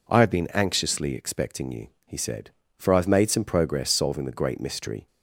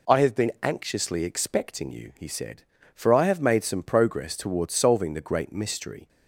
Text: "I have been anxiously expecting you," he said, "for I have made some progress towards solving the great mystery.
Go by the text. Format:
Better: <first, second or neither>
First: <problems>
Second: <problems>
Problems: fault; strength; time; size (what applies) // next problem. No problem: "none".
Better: second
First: skips "towards"; at 3.8 s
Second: none